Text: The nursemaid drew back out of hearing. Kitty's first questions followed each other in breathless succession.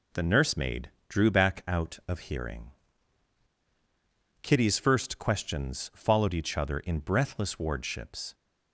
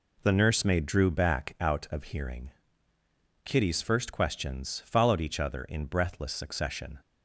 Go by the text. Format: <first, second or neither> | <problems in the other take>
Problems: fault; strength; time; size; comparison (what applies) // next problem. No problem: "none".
second | pauses between "nursemaid" and "drew"; slight; at 0.8 s; 0.18 s long // says "wardships" for "succession"; at 7.5 s